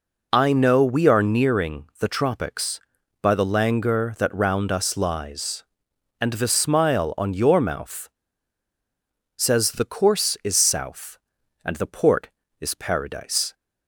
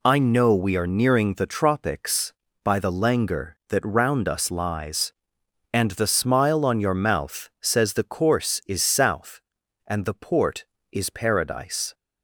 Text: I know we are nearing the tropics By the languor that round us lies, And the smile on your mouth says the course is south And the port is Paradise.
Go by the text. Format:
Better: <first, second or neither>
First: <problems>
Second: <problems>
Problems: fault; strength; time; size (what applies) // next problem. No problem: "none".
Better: second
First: pauses between "nearing" and "the"; slight; at 1.8 s; 0.16 s long // pauses between "mouth" and "says"; strong; at 8.0 s; 1.2 s long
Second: none